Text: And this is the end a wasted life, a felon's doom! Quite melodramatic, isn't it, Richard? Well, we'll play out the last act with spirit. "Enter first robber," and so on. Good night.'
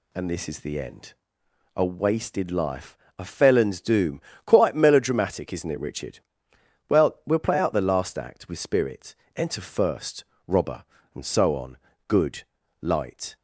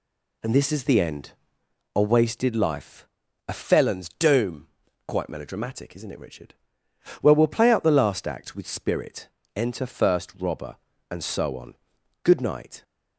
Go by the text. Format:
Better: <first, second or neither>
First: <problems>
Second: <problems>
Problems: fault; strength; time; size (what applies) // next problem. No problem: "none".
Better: second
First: pauses between "end" and "a"; noticeable; at 1.1 s; 0.62 s long // pauses between "first" and "robber"; slight; at 10.2 s; 0.24 s long // says "light" for "night"; at 12.8 s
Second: pauses between "end" and "a"; noticeable; at 1.3 s; 0.64 s long